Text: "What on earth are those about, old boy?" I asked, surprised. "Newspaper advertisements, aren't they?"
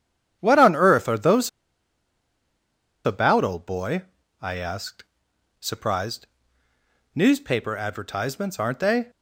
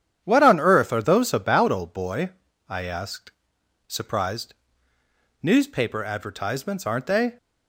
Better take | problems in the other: second | starts louder than the rest; strong; until 1.4 s; 9 dB; strong in the second // pauses between "those" and "about"; strong; at 1.4 s; 1.5 s long

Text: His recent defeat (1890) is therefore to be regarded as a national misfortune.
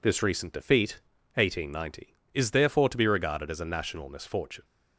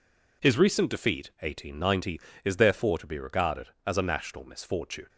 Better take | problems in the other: second | says "This" for "His"; at 0.0 s

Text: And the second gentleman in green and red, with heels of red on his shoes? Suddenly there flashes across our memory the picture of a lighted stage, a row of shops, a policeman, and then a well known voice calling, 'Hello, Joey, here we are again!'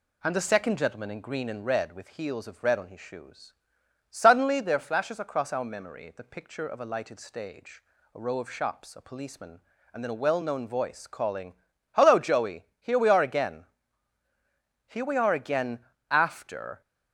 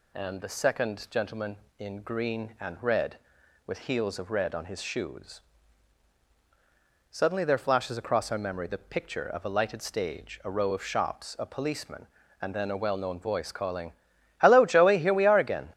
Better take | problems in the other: second | goes on to say "Here we are again after"; strong; from 14.8 s on; 1.9 s long

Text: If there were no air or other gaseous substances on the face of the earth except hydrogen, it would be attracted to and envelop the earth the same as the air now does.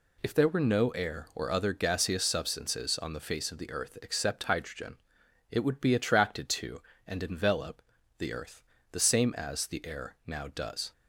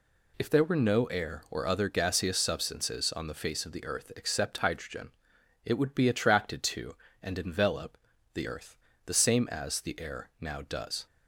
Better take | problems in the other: neither | pauses between "envelop" and "the"; slight; the same in both // pauses between "earth" and "the"; slight; the same in both

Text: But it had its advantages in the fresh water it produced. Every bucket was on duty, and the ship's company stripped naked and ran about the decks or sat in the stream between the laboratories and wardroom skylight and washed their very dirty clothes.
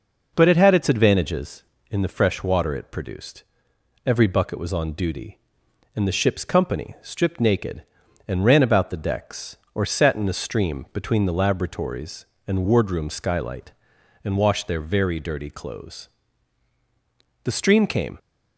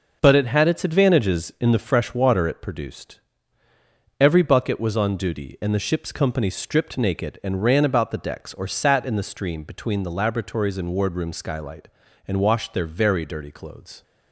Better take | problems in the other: second | goes on to say "The stream came"; noticeable; from 17.4 s on; 0.74 s long

